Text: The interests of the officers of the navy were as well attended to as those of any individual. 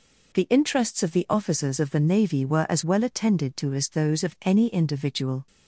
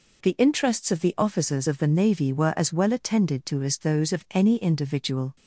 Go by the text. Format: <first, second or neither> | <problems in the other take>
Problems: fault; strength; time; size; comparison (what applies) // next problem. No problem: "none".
neither | none